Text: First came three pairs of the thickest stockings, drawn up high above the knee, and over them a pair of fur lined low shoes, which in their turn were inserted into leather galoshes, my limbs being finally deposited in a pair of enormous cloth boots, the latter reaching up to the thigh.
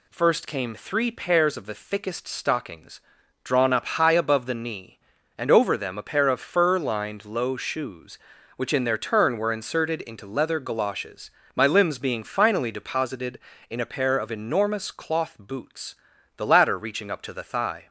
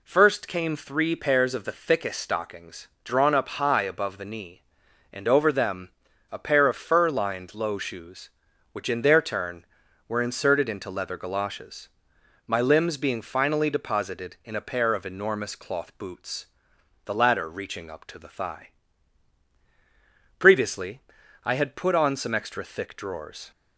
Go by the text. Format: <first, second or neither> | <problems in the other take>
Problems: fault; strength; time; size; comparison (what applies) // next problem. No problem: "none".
first | pauses between "them" and "a"; at 5.8 s; 0.42 s long // goes on to say "Previously I had put on some extra thick drawers"; strong; from 20.3 s on; 3.1 s long